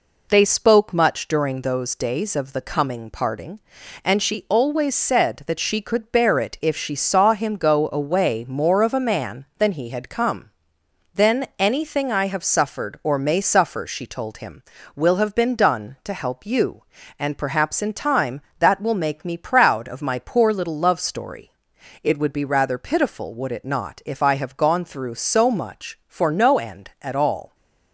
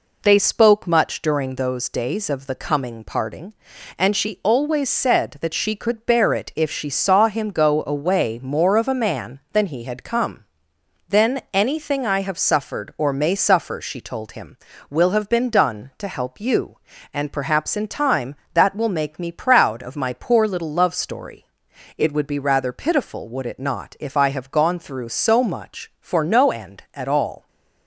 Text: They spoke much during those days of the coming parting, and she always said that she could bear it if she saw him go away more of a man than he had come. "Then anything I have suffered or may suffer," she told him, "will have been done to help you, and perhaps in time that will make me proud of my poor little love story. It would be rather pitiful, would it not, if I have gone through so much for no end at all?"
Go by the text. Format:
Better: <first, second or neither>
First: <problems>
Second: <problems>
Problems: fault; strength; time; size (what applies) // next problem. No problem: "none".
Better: neither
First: none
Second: none